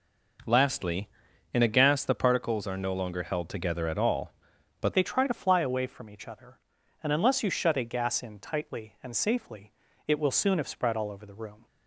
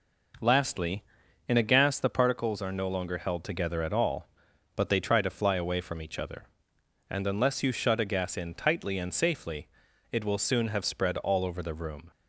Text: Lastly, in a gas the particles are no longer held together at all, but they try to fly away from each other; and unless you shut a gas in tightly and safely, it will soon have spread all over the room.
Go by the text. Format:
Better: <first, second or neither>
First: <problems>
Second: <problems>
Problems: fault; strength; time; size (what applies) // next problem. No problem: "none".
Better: second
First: changes voice at "they"; from 4.9 s on; 6.7 s long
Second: none